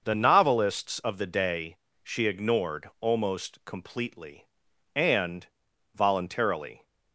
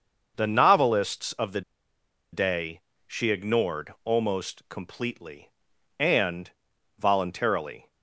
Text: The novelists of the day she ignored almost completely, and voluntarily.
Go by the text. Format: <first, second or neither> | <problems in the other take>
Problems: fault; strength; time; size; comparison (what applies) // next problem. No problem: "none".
first | starts louder than the rest; noticeable; until 1.3 s; 6 dB; noticeable in the first // pauses between "the" and "day"; noticeable; at 1.6 s; 0.72 s long // pauses between "day" and "she"; slight; at 2.7 s; 0.26 s long; slight in the first // pauses between "and" and "voluntarily"; noticeable; at 6.4 s; 0.48 s long; noticeable in the first